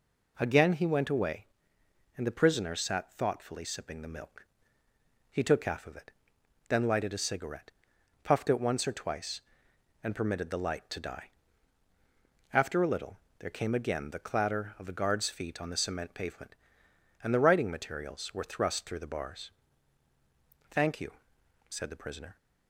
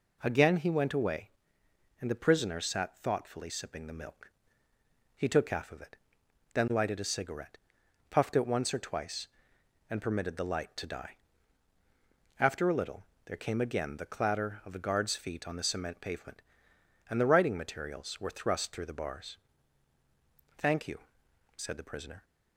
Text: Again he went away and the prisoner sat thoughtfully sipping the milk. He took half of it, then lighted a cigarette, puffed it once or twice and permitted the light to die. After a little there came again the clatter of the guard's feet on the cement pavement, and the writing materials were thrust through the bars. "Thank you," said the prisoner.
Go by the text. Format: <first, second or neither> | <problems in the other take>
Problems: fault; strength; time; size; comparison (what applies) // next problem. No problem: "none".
neither | pauses between "little" and "there"; slight; the same in both